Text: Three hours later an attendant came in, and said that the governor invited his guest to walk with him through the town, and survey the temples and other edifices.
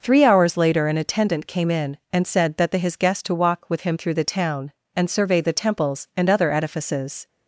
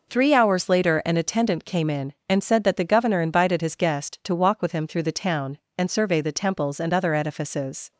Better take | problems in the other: second | skips "governor invited"; at 2.7 s

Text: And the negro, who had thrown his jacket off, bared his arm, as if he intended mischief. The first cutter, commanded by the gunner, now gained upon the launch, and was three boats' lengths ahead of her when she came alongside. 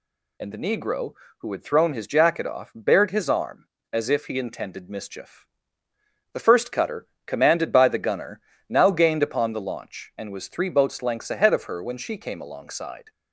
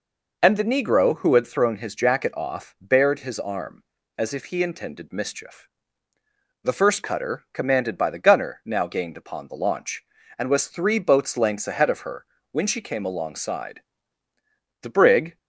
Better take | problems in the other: first | pauses between "her" and "when"; slight; at 12.2 s; 0.28 s long // goes on to say "The brig"; from 14.8 s on; 0.56 s long

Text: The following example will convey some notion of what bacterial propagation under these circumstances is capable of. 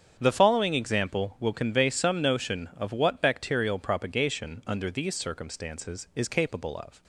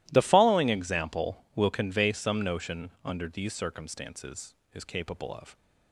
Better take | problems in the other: first | starts louder than the rest; strong; until 1.1 s; 15.5 dB; strong in the first // skips "of what bacterial propagation"; at 2.9 s

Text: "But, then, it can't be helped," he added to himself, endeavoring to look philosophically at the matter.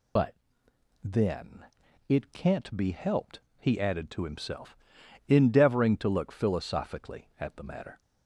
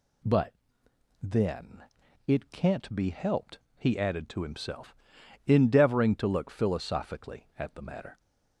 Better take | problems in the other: second | loses the start of "But"; at 0.1 s; 105 ms

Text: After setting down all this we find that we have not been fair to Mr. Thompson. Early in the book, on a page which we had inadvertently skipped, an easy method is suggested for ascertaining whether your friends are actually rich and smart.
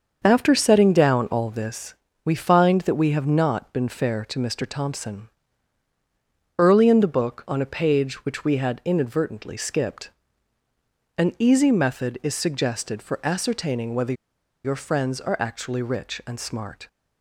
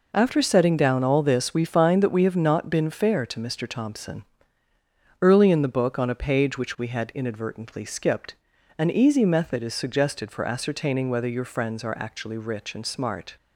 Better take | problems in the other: second | starts louder than the rest; until 1.2 s; 6.5 dB // pauses between "this" and "we"; slight; at 1.9 s; 0.30 s long // pauses between "whether" and "your"; noticeable; at 14.1 s; 0.51 s long

